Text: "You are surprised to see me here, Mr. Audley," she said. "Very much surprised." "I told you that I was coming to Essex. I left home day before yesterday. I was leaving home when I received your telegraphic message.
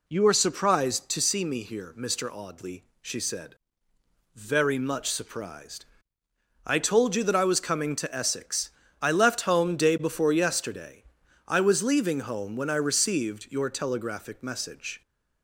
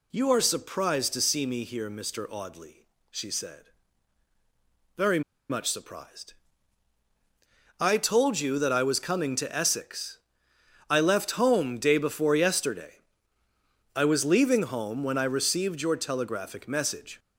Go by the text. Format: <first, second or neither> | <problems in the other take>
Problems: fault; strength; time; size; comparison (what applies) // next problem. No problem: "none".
first | pauses between "Very" and "much"; slight; at 5.2 s; 0.29 s long